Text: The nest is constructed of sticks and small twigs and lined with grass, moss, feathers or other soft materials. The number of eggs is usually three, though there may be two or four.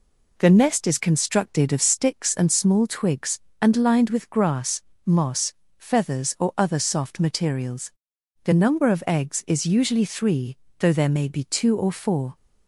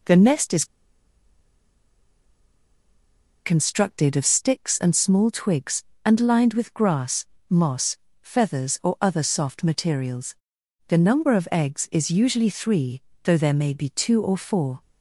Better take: first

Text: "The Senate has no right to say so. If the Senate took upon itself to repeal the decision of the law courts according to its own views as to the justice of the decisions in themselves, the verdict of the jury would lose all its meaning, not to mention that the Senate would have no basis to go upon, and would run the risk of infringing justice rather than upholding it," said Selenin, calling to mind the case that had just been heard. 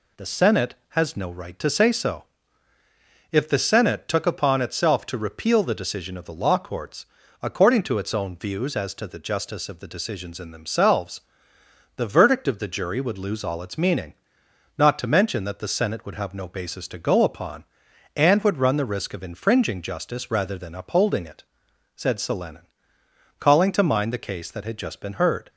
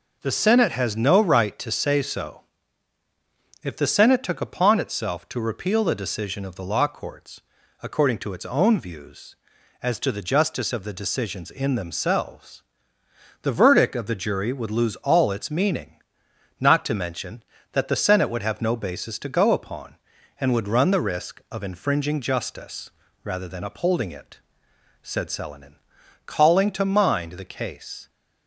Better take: first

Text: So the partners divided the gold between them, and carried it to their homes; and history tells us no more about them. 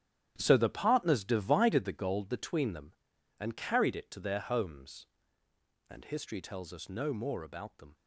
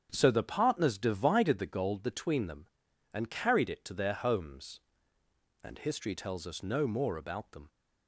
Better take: second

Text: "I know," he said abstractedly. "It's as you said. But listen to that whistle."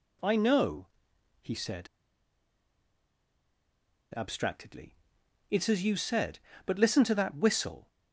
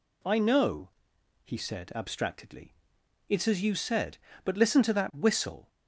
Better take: second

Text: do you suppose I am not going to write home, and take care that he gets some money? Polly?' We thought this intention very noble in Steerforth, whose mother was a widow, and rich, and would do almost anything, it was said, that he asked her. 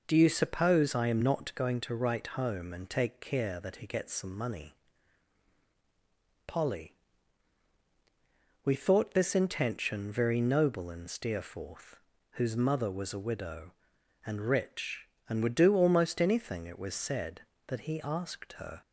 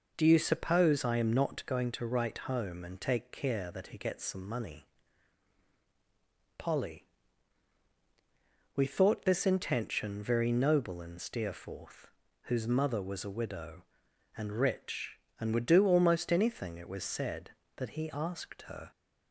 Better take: neither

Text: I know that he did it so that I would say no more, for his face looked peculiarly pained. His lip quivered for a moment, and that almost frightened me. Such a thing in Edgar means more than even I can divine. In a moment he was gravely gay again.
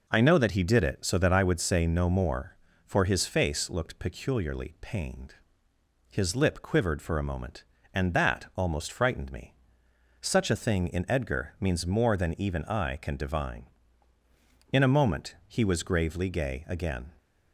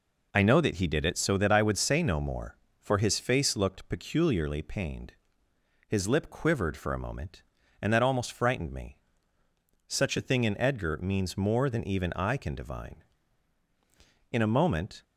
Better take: first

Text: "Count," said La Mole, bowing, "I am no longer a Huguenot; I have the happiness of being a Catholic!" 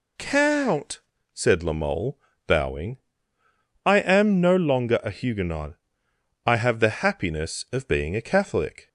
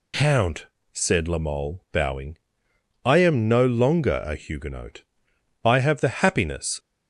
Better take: first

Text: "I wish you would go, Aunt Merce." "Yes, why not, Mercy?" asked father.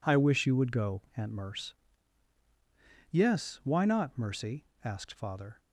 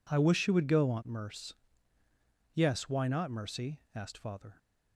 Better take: neither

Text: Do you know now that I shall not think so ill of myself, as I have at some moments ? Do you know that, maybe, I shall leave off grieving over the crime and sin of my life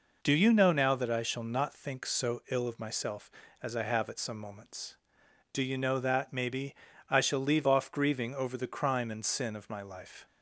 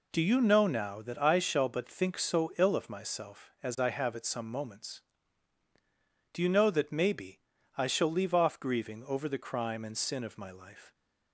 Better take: first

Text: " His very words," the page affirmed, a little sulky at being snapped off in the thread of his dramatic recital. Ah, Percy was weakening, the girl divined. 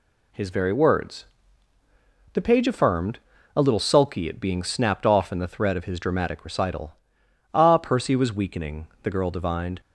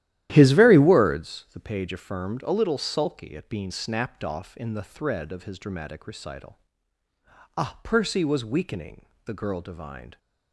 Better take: first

